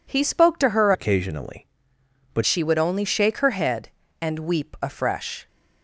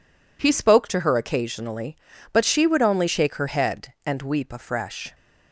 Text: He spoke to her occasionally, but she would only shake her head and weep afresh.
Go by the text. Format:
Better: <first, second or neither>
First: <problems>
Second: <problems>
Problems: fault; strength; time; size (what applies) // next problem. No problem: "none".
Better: second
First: changes voice from "occasionally" to "but"; from 0.9 to 2.4 s; 1.5 s long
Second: none